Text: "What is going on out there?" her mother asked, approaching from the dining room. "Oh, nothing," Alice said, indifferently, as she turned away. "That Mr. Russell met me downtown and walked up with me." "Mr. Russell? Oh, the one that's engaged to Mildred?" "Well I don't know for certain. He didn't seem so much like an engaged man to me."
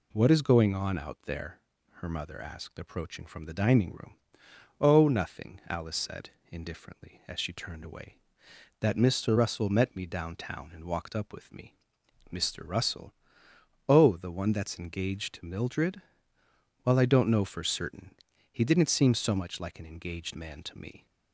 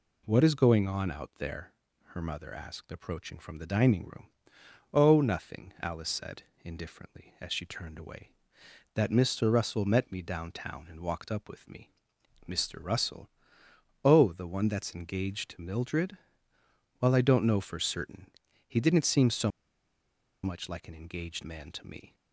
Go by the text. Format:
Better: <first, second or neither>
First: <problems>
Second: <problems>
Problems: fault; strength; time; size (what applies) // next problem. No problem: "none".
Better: first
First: none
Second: pauses between "so" and "much"; noticeable; at 19.5 s; 0.93 s long